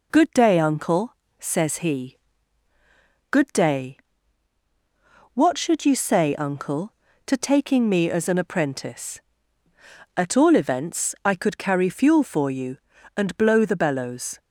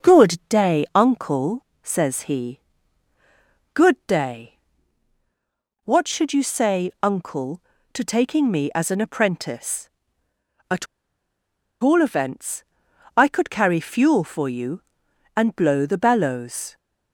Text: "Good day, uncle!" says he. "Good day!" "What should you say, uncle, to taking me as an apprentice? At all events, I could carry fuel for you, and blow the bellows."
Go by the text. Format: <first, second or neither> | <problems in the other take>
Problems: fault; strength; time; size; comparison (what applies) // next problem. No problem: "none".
first | pauses between "At" and "all"; noticeable; at 10.8 s; 0.97 s long